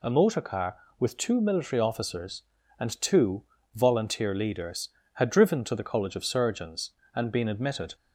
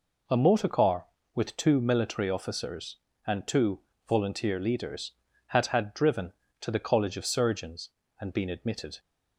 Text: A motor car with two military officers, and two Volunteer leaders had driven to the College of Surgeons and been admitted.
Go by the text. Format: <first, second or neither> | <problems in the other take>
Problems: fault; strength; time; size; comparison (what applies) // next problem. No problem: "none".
first | pauses between "two" and "Volunteer"; slight; at 3.8 s; 0.26 s long; slight in the first // says "had" twice; at 5.6 s